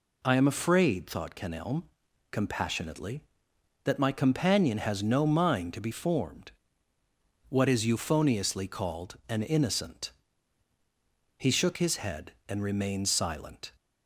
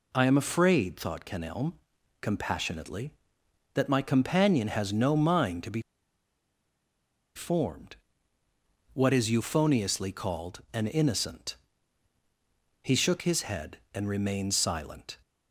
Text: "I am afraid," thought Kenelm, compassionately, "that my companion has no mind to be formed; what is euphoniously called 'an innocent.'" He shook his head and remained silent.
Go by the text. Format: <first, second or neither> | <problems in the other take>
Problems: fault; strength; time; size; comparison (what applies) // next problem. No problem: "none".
first | pauses between "be" and "formed"; strong; at 5.7 s; 1.5 s long